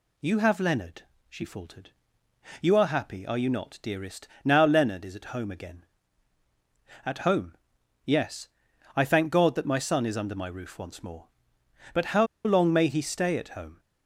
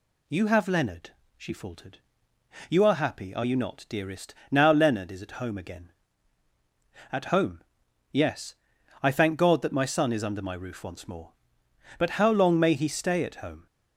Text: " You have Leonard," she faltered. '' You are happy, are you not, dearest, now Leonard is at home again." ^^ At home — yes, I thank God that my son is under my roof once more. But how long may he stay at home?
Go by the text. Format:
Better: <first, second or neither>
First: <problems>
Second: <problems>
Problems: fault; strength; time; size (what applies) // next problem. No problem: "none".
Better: second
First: pauses between "how" and "long"; slight; at 12.2 s; 0.19 s long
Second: none